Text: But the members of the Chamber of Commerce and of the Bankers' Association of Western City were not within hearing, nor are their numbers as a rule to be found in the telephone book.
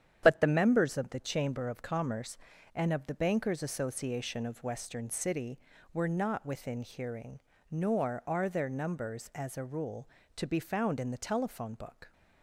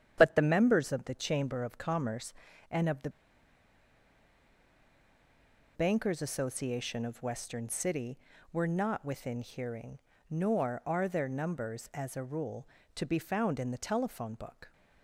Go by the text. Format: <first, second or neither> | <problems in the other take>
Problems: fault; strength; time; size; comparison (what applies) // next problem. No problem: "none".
first | starts louder than the rest; strong; until 1.1 s; 9.5 dB; strong in the first // pauses between "the" and "Bankers"; strong; at 3.0 s; 2.6 s long